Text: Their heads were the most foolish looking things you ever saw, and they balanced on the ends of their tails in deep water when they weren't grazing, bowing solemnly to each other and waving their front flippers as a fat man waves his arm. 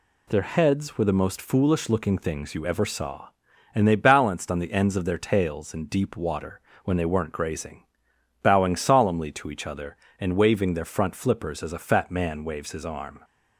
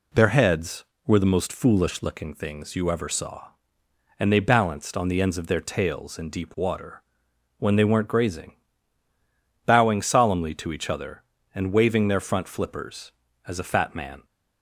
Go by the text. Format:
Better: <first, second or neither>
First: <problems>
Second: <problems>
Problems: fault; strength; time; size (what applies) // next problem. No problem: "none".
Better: first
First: pauses between "water" and "when"; slight; at 6.5 s; 0.24 s long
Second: pauses between "water" and "when"; noticeable; at 7.0 s; 0.58 s long // stops before "waves his arm"; at 14.2 s